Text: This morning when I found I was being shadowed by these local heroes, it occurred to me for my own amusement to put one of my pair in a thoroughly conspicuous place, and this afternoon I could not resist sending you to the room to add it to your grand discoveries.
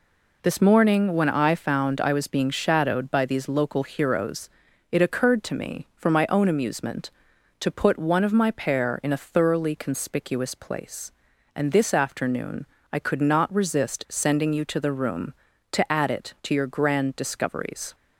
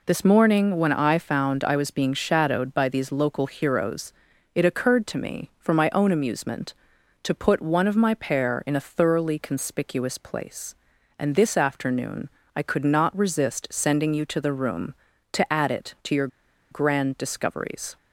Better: first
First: pauses between "afternoon" and "I"; slight; at 12.6 s; 0.24 s long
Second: pauses between "afternoon" and "I"; slight; at 12.2 s; 0.24 s long // pauses between "your" and "grand"; at 16.2 s; 0.44 s long

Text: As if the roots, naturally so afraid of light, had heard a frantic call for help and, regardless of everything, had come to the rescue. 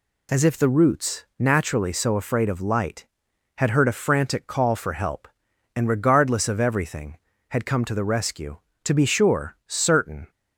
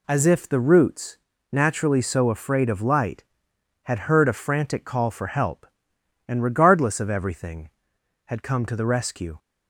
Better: second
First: goes on to say "To be sure certain"; from 8.8 s on; 1.4 s long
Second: none

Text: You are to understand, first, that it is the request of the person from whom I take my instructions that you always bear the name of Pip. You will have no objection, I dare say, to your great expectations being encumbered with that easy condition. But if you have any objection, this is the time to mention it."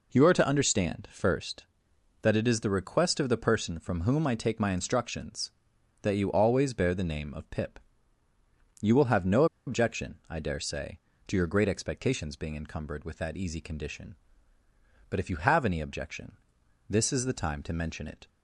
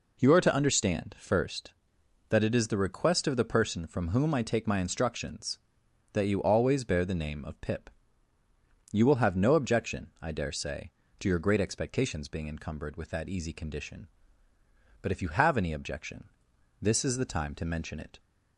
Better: second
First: pauses between "no" and "objection"; slight; at 9.4 s; 0.21 s long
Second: none

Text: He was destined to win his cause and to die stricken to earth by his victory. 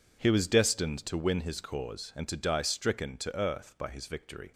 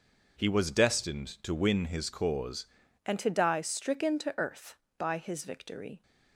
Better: first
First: none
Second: changes voice at "and"; from 3.0 s on; 3.0 s long

